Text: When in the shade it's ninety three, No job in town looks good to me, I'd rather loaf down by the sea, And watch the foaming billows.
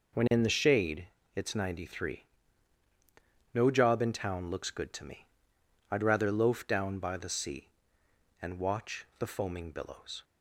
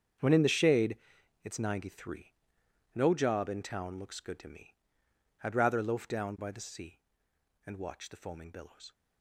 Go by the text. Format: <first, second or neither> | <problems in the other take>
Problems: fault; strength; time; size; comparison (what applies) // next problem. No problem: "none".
first | gets quieter; strong; throughout; 15.5 dB // pauses between "shade" and "it's"; noticeable; at 0.9 s; 0.48 s long; slight in the first